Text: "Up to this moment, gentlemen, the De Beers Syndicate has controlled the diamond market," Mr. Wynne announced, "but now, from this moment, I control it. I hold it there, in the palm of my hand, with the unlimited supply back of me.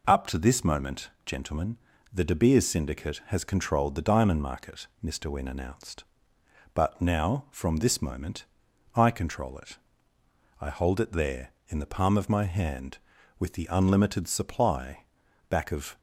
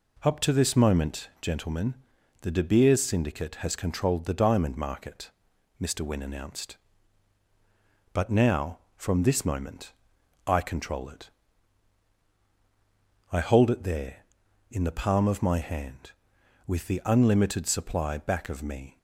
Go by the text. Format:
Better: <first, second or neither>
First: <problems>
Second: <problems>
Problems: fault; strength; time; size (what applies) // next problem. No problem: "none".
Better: second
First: pauses between "supply" and "back"; at 15.0 s; 0.44 s long // stops before "me"; at 15.9 s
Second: none